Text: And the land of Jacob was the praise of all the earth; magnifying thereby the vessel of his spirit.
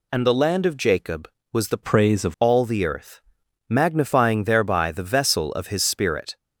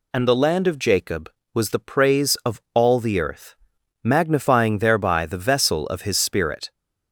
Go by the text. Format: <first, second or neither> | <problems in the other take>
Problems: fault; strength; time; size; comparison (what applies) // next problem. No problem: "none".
second | changes voice from "praise" to "of"; from 1.8 to 2.3 s; 0.5 s long